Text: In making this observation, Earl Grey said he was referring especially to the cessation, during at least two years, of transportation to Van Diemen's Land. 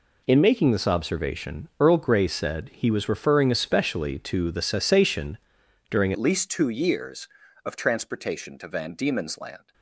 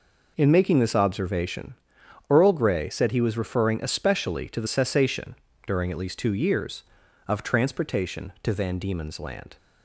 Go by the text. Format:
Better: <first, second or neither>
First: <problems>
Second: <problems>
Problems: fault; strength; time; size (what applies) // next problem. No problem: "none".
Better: second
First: changes voice at "at"; from 6.1 s on; 3.6 s long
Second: none